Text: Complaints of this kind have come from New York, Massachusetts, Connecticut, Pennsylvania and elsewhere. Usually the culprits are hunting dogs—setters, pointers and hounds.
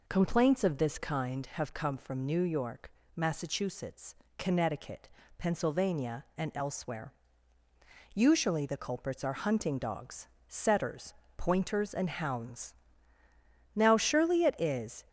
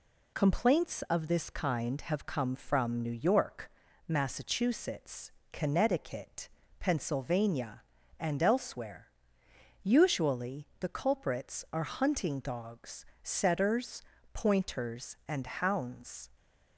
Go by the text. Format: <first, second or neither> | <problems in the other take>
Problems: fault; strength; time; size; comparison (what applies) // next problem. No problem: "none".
second | goes on to say "Now surely it is"; from 13.7 s on; 1.3 s long